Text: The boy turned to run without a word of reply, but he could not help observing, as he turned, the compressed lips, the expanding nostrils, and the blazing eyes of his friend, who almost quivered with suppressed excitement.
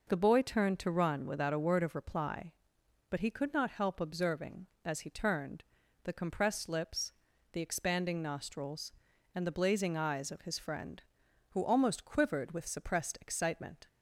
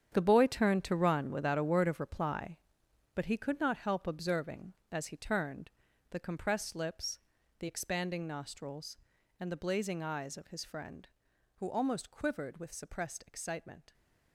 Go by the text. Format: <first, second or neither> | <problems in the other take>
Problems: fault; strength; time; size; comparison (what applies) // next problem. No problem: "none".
first | gets quieter; strong; throughout; 12.5 dB